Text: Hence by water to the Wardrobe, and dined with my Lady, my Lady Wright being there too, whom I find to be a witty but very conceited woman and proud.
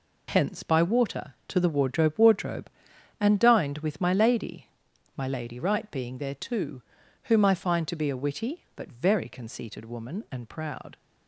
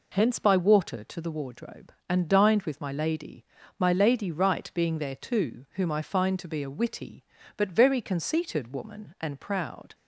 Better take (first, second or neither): second